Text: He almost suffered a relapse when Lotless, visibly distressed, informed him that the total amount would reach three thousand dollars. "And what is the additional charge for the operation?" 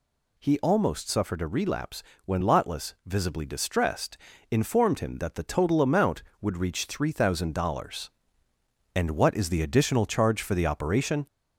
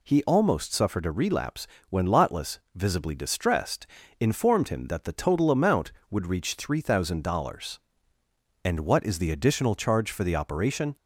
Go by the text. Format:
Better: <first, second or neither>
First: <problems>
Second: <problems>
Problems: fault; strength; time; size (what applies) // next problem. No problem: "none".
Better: second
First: gets louder; slight; throughout; 3 dB // pauses between "relapse" and "when"; slight; at 2.0 s; 0.22 s long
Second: pauses between "relapse" and "when"; slight; at 1.6 s; 0.22 s long